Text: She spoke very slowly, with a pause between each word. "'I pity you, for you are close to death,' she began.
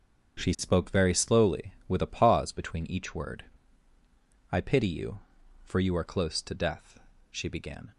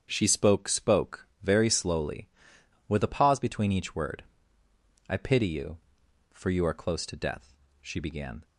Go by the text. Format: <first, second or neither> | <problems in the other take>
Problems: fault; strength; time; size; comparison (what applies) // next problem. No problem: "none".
first | starts louder than the rest; strong; until 1.1 s; 7.5 dB; also in the first // says "spoke" twice; at 0.6 s